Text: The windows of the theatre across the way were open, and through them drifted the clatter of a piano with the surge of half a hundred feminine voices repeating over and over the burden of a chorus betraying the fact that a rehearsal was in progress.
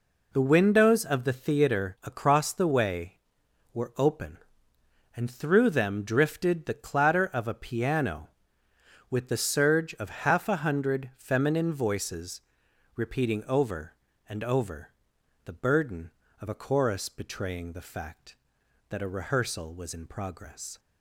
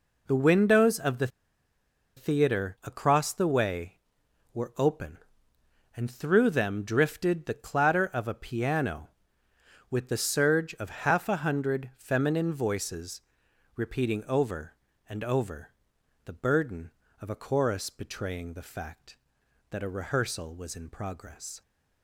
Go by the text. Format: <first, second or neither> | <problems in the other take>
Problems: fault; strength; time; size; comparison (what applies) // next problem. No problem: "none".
first | pauses between "the" and "theatre"; noticeable; at 1.2 s; 0.88 s long // pauses between "voices" and "repeating"; noticeable; at 13.1 s; 0.56 s long; noticeable in the first // pauses between "over" and "the"; noticeable; at 15.7 s; 0.52 s long; noticeable in the first